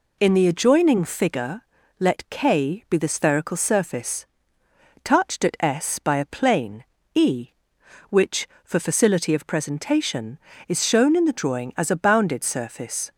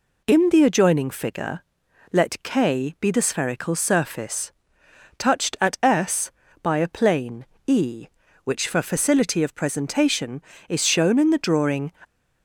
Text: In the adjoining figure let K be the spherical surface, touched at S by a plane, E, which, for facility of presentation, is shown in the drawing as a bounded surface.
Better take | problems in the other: first | pauses between "figure" and "let"; noticeable; at 1.6 s; 0.50 s long; slight in the first // stops before "as a bounded surface"; at 12.0 s

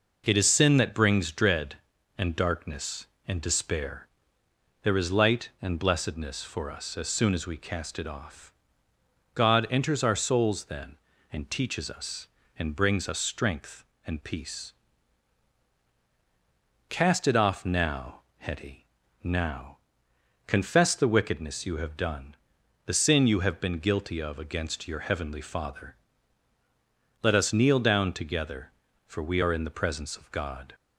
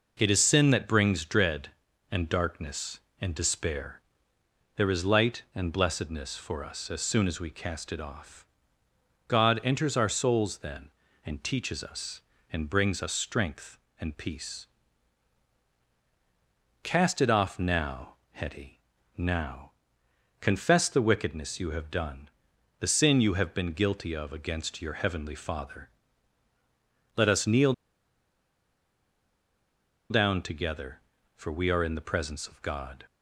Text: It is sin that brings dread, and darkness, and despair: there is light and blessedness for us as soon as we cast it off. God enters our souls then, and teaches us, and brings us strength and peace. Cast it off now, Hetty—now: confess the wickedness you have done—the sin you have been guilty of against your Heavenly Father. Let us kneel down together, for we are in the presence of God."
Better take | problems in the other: first | pauses between "kneel" and "down"; strong; at 27.7 s; 2.3 s long

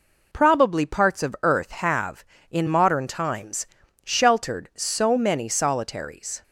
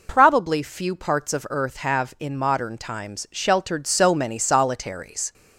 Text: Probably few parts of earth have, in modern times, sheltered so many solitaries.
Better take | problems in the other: second | skips "few"; at 0.8 s

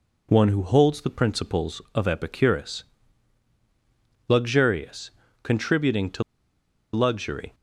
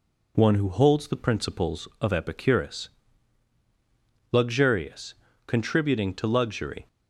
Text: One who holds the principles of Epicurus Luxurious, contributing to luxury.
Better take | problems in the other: second | pauses between "Epicurus" and "Luxurious"; strong; at 2.8 s; 1.4 s long; strong in the second // pauses between "to" and "luxury"; noticeable; at 6.2 s; 0.71 s long

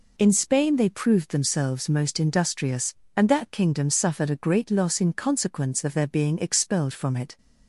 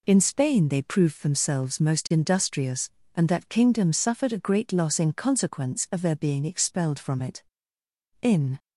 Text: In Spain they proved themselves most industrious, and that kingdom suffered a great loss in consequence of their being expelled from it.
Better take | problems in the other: first | goes on to say "In"; slight; from 8.2 s on; 0.38 s long

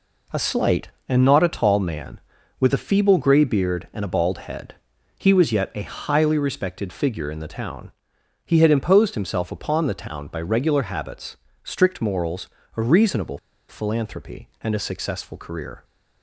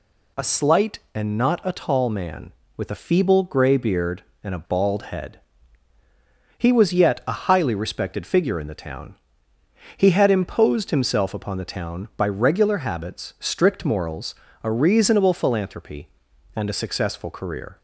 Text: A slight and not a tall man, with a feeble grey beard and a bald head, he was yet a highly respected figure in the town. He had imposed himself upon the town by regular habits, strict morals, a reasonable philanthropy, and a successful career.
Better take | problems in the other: second | pauses between "reasonable" and "philanthropy"; slight; at 13.3 s; 0.30 s long

